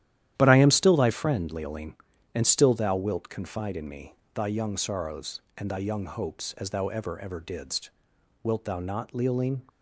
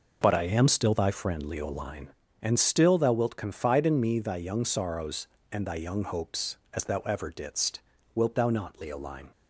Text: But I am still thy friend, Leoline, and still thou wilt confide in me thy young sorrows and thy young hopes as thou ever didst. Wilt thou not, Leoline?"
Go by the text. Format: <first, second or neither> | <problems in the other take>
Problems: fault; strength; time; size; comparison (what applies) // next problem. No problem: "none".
second | starts louder than the rest; strong; until 1.3 s; 12 dB // pauses between "me" and "thy"; slight; at 4.1 s; 0.20 s long // says "ever" twice; at 7.1 s